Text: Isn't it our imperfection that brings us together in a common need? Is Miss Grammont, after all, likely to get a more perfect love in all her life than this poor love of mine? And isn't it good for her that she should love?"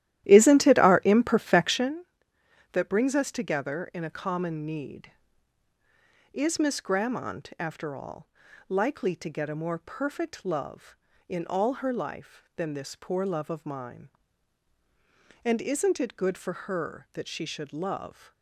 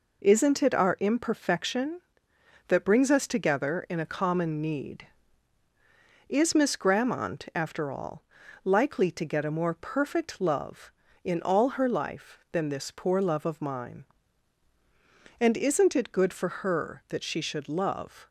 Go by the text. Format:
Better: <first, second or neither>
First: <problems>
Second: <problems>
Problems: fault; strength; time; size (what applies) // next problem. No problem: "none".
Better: second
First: starts louder than the rest; strong; until 2.0 s; 13 dB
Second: none